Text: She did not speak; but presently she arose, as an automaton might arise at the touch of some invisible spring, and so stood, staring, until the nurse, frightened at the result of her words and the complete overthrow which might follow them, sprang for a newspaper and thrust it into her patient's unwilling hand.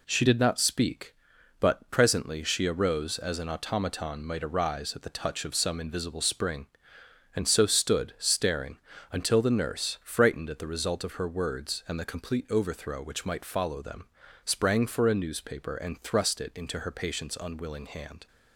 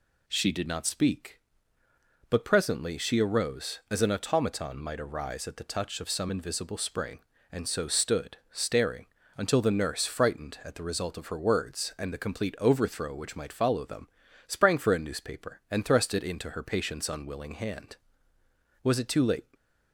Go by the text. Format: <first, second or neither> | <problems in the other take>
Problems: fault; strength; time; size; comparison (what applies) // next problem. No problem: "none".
first | goes on to say "Was it too late"; noticeable; from 18.8 s on; 0.72 s long // stays silent after the last word; slight; from 19.4 s on; 0.5 s long